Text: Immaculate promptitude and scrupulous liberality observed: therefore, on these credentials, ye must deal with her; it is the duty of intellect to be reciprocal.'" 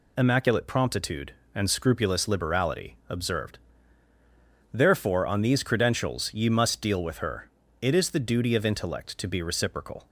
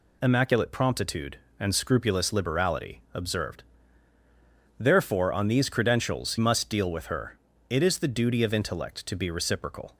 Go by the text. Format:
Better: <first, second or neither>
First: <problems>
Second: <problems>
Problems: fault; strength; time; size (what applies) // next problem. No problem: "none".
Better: first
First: none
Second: skips "ye"; at 6.3 s